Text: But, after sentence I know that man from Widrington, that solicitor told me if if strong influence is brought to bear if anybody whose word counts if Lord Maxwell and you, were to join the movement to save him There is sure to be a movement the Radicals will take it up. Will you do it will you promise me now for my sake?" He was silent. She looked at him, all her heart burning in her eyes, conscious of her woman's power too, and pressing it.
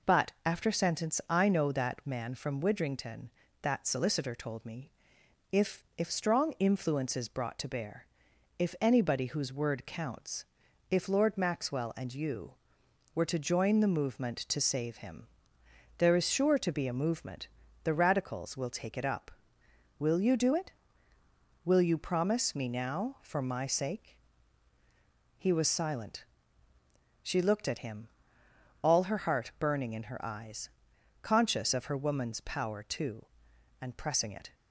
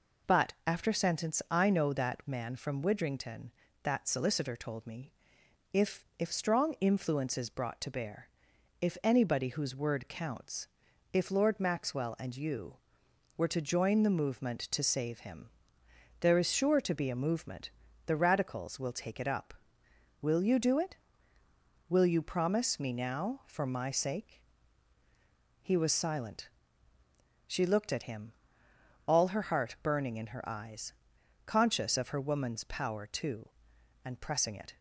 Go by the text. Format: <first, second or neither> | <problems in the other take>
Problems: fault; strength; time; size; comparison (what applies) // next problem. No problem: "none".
neither | pauses between "me" and "if"; noticeable; the same in both // pauses between "bear" and "if"; noticeable; the same in both // pauses between "counts" and "if"; the same in both // pauses between "him" and "There"; noticeable; the same in both // pauses between "movement" and "the"; the same in both